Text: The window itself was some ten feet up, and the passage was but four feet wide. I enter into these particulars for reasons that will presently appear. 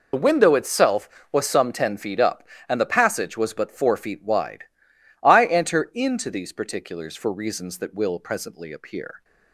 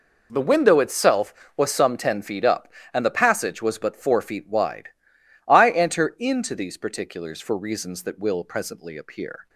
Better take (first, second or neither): second